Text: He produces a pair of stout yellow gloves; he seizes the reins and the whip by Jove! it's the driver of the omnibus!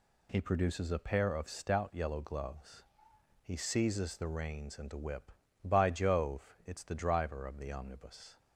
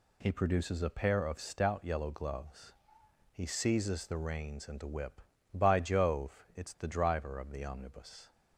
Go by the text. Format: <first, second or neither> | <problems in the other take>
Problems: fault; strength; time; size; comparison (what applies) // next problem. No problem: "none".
neither | none